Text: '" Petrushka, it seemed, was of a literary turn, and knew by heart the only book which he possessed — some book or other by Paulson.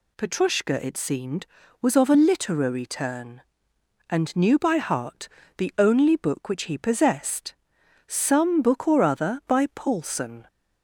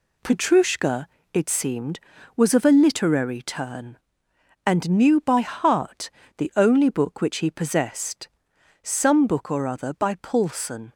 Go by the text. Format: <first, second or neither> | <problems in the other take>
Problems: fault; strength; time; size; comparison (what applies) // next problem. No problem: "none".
first | gets quieter; noticeable; throughout; 5.5 dB // pauses between "heart" and "the"; slight; at 6.1 s; 0.28 s long; slight in the first